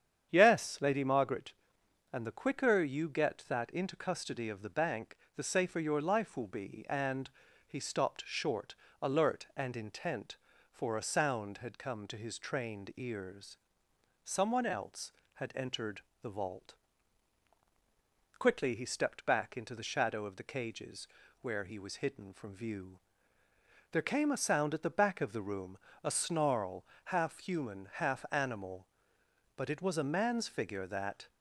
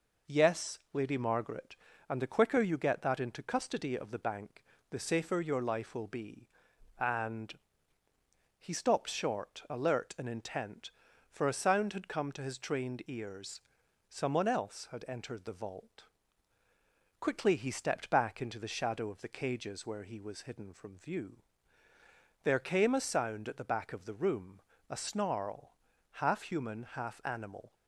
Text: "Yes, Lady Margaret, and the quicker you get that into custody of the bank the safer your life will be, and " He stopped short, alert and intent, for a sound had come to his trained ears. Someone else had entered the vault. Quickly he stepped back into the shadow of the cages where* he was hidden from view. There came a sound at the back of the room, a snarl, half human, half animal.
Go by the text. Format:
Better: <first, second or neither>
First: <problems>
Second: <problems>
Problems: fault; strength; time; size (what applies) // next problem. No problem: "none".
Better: second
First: starts louder than the rest; strong; until 1.3 s; 8.5 dB // pauses between "bank" and "the"; slight; at 5.1 s; 0.18 s long // pauses between "entered" and "the"; slight; at 16.0 s; 0.20 s long // pauses between "cages" and "where"; slight; at 21.0 s; 0.34 s long // goes on to say "But it was a man's figure that"; strong; from 29.5 s on; 1.7 s long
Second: pauses between "bank" and "the"; slight; at 4.6 s; 0.26 s long